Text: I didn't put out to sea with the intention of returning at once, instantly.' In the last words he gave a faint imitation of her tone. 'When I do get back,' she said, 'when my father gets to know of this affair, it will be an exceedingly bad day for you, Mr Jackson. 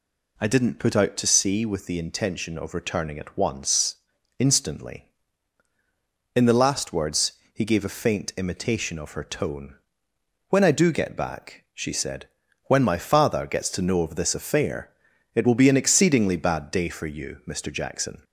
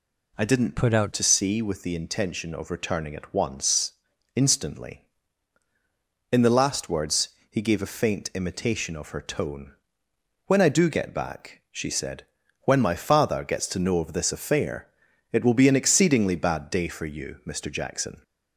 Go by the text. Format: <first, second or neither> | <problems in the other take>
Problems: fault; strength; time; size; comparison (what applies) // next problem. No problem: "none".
first | changes voice from "put" to "out"; from 0.7 to 1.1 s; 0.4 s long // pauses between "words" and "he"; slight; at 7.2 s; 0.22 s long; slight in the first